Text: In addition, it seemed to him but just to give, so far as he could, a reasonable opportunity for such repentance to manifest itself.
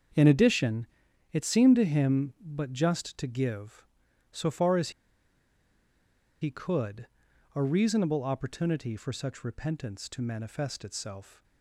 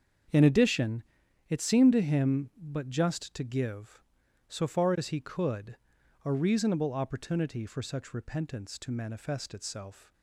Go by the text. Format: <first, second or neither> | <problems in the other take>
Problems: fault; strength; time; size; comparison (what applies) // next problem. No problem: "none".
second | starts louder than the rest; strong; until 1.6 s; 7 dB; strong in the second // pauses between "as" and "he"; strong; at 4.9 s; 1.5 s long